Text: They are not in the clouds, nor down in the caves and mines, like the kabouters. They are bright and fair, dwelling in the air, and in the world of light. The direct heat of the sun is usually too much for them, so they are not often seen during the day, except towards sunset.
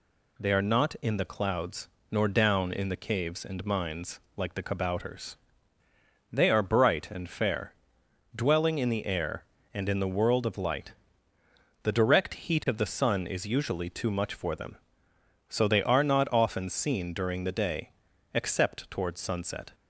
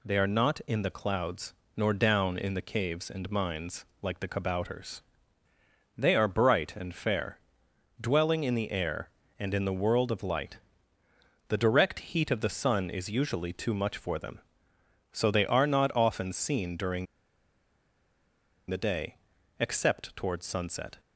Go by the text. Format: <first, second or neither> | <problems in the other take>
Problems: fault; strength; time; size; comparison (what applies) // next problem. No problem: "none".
first | pauses between "during" and "the"; strong; at 17.0 s; 1.6 s long